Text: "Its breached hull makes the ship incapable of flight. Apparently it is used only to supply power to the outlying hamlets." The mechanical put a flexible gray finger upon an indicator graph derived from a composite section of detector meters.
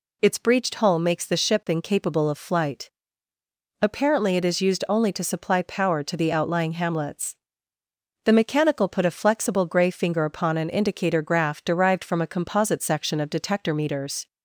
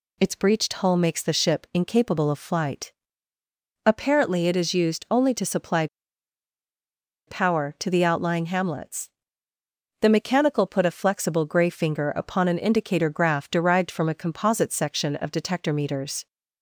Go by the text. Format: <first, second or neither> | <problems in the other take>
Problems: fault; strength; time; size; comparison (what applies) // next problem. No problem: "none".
first | pauses between "supply" and "power"; strong; at 5.8 s; 1.4 s long